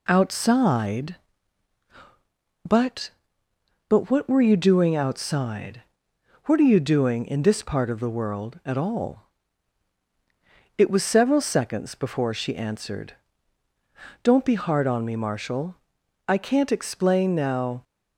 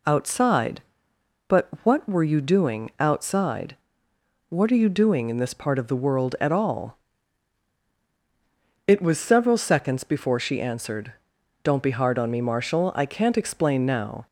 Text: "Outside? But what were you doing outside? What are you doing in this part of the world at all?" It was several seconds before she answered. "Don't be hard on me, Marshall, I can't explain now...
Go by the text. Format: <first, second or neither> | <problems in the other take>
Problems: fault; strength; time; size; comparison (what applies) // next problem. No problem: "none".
second | says "But" twice; at 3.8 s